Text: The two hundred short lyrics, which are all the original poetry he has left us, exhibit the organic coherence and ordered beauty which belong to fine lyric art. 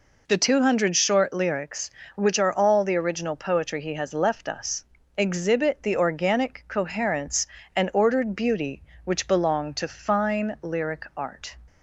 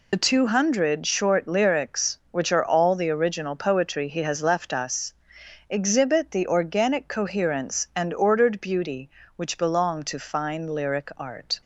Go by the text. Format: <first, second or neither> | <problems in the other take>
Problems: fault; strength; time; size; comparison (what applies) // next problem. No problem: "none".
first | loses the start of "The"; at 0.1 s; 40 ms